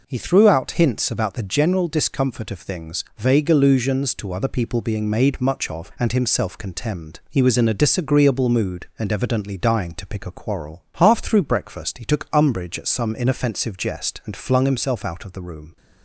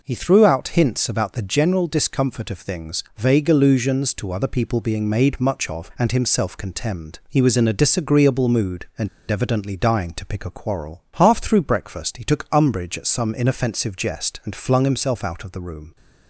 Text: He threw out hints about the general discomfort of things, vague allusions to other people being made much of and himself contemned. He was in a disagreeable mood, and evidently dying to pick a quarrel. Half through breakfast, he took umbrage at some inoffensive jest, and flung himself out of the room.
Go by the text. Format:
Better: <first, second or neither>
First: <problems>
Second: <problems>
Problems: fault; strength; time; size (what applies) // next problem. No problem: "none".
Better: first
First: none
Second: pauses between "and" and "evidently"; slight; at 9.0 s; 0.22 s long